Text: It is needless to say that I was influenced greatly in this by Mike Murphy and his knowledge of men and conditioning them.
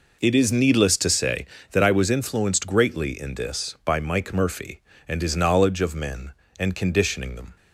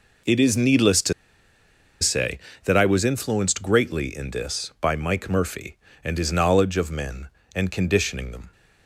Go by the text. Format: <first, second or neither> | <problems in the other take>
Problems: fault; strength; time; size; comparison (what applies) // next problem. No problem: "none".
first | pauses between "to" and "say"; noticeable; at 1.1 s; 0.88 s long